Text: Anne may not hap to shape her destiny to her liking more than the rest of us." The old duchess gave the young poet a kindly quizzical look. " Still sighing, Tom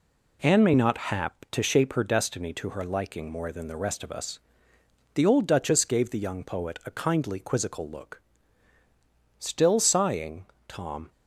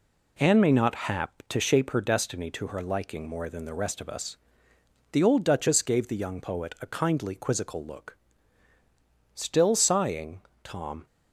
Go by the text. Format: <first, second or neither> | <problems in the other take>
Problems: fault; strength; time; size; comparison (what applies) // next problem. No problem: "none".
neither | none